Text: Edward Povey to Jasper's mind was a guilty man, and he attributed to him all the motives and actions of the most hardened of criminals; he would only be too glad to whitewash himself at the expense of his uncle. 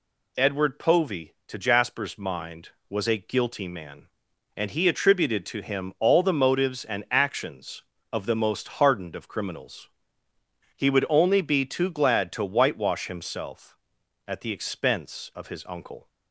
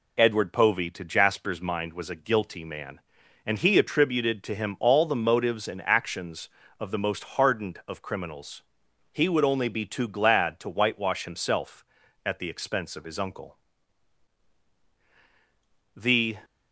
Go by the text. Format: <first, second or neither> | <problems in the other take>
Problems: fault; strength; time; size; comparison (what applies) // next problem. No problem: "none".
first | goes on to say "The"; slight; from 15.9 s on; 0.44 s long